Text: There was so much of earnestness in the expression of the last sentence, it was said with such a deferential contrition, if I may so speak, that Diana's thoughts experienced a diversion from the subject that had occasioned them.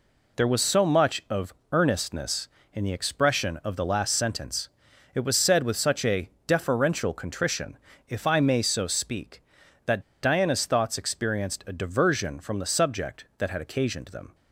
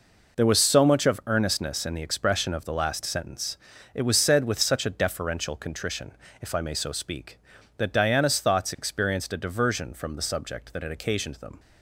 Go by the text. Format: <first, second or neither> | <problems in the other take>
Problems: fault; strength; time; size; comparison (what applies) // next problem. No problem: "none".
second | pauses between "of" and "earnestness"; slight; at 1.5 s; 0.18 s long // pauses between "a" and "deferential"; slight; at 6.2 s; 0.18 s long // pauses between "that" and "Diana's"; slight; at 10.0 s; 0.19 s long